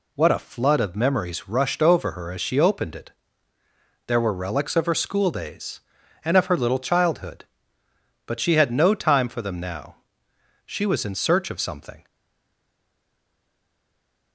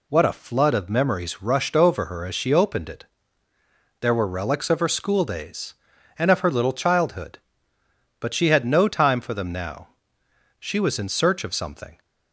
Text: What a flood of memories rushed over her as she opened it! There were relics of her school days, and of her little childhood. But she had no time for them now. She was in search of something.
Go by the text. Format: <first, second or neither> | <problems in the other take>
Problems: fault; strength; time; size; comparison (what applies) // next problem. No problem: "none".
second | stays silent after the last word; from 12.0 s on; 2.3 s long